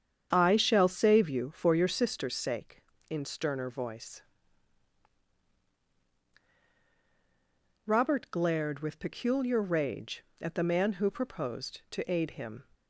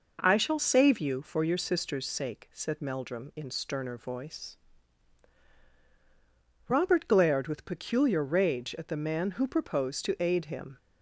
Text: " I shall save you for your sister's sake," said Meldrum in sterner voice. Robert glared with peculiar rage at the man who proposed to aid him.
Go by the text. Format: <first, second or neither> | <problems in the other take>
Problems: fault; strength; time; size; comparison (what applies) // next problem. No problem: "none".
second | starts louder than the rest; strong; until 1.3 s; 8 dB // skips "said Meldrum"; at 2.9 s